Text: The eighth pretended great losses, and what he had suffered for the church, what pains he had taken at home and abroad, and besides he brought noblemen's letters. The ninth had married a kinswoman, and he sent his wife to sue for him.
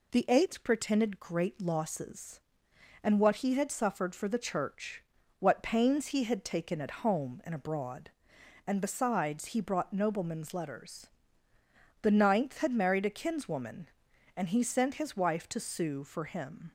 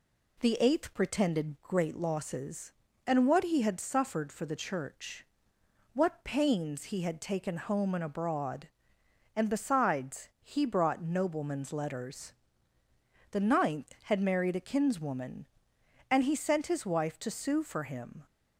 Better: first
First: none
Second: skips "at"; at 7.5 s

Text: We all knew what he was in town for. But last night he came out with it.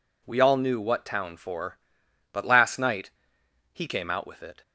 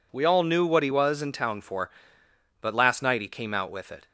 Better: second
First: skips "he was in"; at 1.0 s // pauses between "night" and "he"; noticeable; at 3.0 s; 0.64 s long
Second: none

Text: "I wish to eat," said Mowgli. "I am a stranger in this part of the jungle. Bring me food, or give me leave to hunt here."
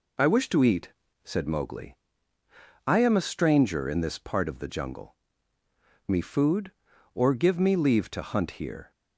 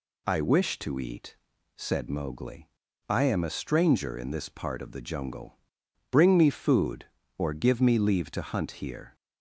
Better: second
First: skips "Bring"; at 5.6 s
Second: none

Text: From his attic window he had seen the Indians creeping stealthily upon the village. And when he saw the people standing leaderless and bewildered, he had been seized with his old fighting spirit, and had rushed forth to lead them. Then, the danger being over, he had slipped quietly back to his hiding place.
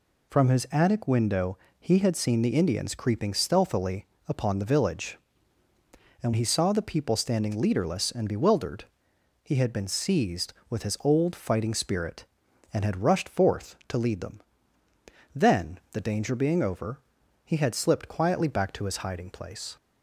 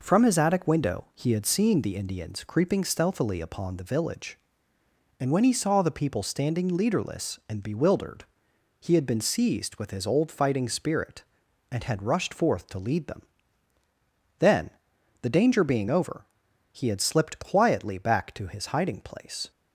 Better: second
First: pauses between "window" and "he"; slight; at 1.5 s; 0.22 s long // pauses between "stealthily" and "upon"; slight; at 4.0 s; 0.22 s long // skips "when"; at 6.3 s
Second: none

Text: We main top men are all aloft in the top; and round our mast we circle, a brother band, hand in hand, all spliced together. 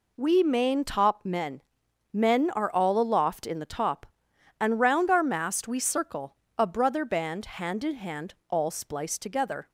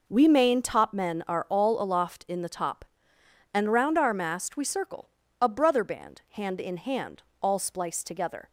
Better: second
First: says "men" twice; at 2.1 s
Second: none

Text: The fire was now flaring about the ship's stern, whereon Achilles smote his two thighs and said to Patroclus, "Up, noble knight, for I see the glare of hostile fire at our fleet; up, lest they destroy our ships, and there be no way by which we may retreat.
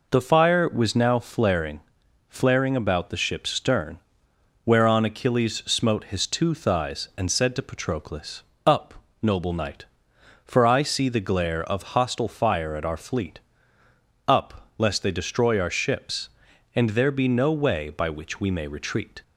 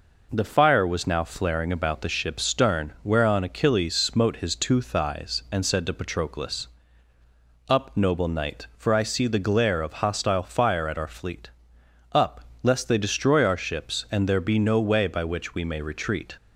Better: second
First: says "flaring" twice; at 2.2 s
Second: none

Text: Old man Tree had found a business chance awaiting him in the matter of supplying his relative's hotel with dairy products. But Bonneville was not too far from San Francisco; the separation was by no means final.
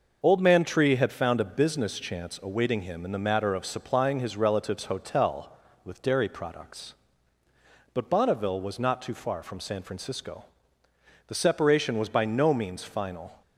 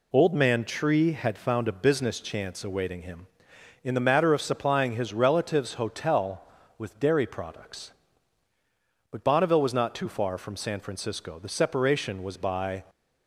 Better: first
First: none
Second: stops before "no means final"; at 12.8 s

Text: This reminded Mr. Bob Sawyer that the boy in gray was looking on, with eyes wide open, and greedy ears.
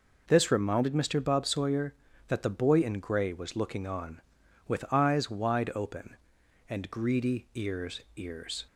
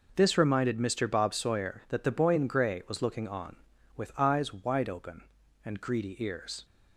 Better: second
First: says "ears" twice; at 8.1 s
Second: none

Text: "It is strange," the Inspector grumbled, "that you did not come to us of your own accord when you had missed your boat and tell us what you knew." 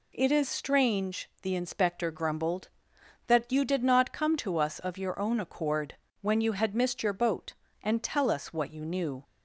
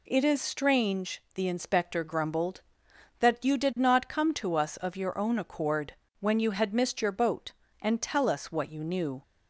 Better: neither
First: pauses between "accord" and "when"; slight; at 5.9 s; 0.24 s long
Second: pauses between "accord" and "when"; slight; at 5.9 s; 0.24 s long

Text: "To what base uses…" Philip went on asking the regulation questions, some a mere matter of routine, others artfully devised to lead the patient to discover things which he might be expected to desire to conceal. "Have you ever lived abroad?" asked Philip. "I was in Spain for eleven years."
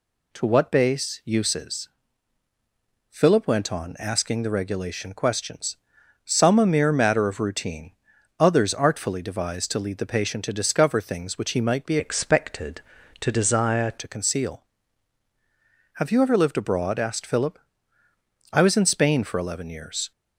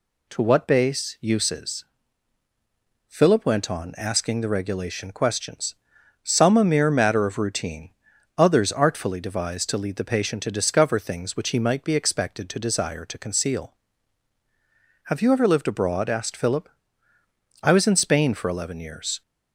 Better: second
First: changes voice from "expected" to "desire"; from 11.9 to 13.9 s; 2.0 s long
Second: none

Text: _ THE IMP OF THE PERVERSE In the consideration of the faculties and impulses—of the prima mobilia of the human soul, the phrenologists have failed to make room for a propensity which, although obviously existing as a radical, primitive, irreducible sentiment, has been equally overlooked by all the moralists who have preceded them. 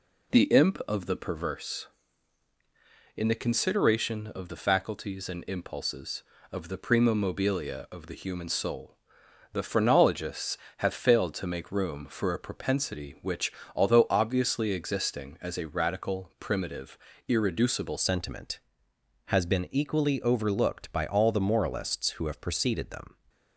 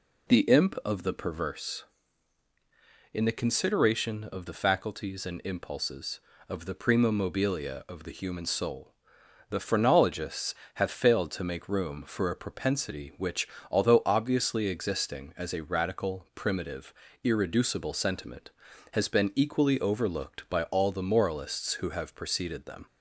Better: second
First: changes voice at "sentiment"; from 17.9 s on; 5.2 s long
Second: none

